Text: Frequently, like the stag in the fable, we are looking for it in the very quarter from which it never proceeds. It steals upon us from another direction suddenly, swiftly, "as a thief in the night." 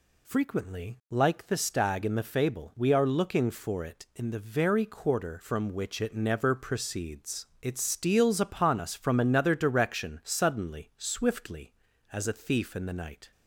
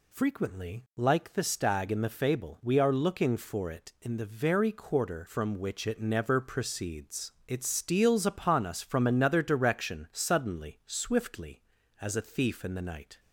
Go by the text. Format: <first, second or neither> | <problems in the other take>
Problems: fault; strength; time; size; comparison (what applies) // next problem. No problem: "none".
neither | none